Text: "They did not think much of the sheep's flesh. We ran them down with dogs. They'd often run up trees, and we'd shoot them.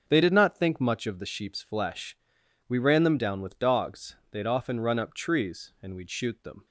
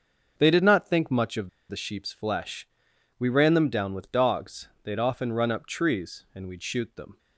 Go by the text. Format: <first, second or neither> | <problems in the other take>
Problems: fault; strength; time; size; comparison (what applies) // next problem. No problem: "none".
first | starts louder than the rest; until 1.3 s; 6.5 dB; also in the first // pauses between "of" and "the"; slight; at 1.4 s; 0.21 s long